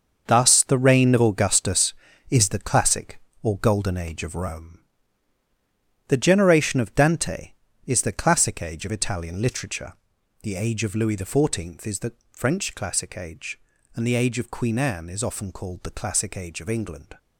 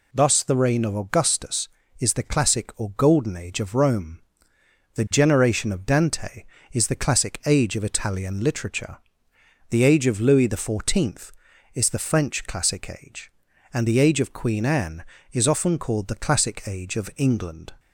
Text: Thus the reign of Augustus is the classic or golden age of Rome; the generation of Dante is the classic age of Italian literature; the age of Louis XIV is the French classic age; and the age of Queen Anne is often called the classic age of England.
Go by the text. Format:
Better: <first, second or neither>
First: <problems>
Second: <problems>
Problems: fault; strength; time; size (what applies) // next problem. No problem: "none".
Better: second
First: gets quieter; strong; throughout; 10 dB // pauses between "the" and "French"; slight; at 12.1 s; 0.20 s long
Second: none